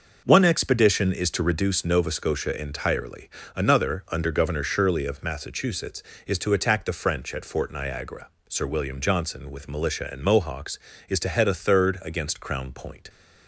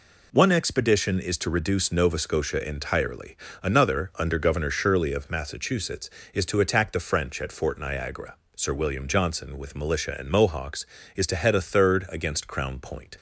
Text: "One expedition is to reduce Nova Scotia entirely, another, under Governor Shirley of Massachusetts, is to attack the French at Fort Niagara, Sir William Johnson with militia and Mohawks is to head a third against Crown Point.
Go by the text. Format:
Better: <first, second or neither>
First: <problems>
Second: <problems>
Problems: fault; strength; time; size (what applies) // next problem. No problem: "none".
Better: second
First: starts louder than the rest; noticeable; until 1.7 s; 6 dB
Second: none